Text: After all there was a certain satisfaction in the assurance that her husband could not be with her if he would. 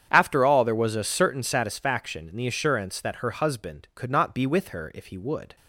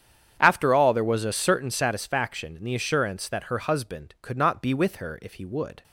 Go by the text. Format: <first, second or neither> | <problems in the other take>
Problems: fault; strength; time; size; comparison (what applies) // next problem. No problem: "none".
neither | starts louder than the rest; strong; the same in both